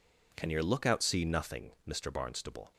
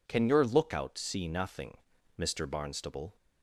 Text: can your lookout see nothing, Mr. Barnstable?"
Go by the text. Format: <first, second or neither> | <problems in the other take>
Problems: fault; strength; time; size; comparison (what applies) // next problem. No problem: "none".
neither | none